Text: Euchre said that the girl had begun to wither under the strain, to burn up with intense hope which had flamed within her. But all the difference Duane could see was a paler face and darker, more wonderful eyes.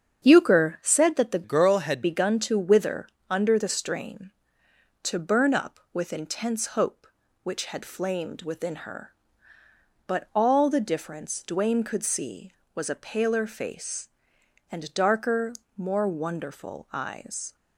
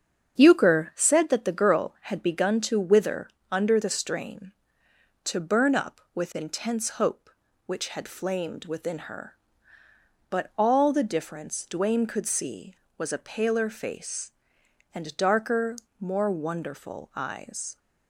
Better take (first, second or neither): second